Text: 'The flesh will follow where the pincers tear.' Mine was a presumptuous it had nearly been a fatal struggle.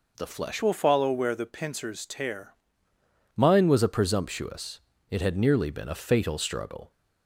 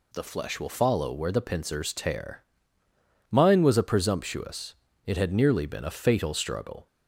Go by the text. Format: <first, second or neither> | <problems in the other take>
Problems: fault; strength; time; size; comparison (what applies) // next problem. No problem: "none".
second | changes voice from "will" to "tear"; from 0.6 to 2.5 s; 1.9 s long // pauses between "presumptuous" and "it"; slight; at 4.7 s; 0.32 s long; slight in the second